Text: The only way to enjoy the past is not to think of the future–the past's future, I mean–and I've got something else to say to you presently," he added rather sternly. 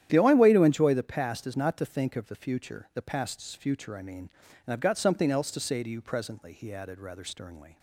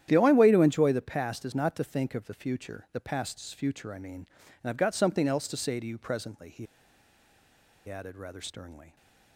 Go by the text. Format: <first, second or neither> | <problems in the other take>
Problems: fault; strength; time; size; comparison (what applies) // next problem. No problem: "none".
first | starts louder than the rest; strong; until 1.1 s; 10.5 dB; strong in the first // pauses between "he" and "added"; at 6.6 s; 1.2 s long